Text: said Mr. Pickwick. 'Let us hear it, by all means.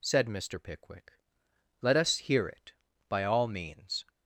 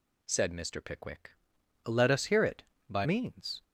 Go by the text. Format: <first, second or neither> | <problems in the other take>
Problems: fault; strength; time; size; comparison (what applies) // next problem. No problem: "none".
first | skips "all"; at 3.0 s